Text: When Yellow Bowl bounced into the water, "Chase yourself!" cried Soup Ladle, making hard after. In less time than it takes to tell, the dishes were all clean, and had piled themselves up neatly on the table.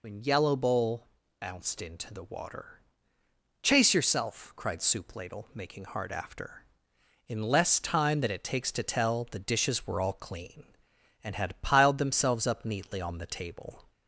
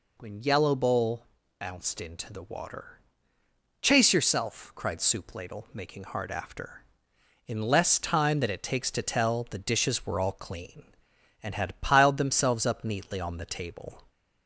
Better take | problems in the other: second | loses the start of "When"; at 0.0 s; 40 ms // pauses between "Bowl" and "bounced"; slight; at 1.0 s; 0.32 s long; slight in the second

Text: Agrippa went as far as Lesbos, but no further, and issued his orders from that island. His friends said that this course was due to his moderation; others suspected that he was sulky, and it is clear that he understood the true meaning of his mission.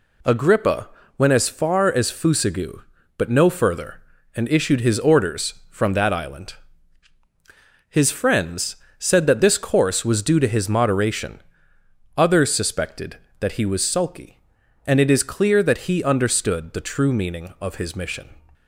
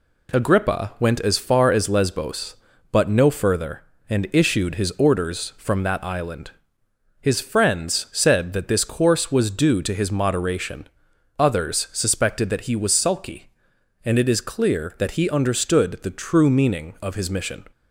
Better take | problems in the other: second | pauses between "Agrippa" and "went"; slight; at 0.8 s; 0.30 s long // says "Fusagu" for "Lesbos"; at 2.1 s // pauses between "friends" and "said"; slight; at 8.7 s; 0.24 s long

